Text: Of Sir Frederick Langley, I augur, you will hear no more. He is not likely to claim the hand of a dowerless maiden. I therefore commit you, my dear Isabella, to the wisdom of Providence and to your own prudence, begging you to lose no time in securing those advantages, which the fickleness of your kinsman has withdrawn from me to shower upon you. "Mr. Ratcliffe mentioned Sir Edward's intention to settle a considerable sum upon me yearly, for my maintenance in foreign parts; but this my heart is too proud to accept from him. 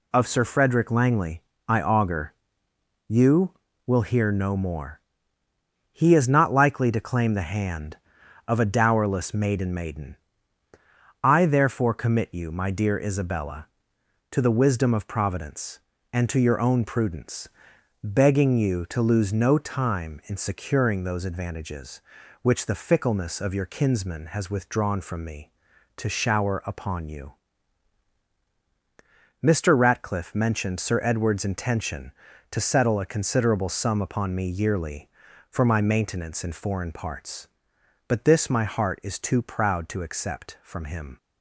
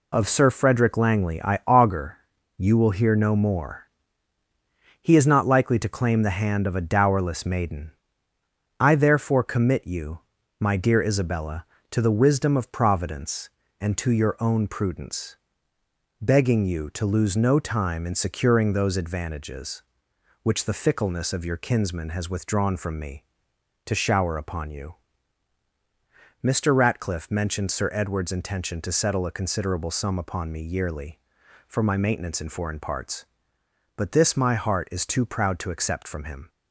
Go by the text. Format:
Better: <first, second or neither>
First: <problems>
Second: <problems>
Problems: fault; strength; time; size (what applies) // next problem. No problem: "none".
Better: second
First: says "maiden" twice; at 9.7 s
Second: none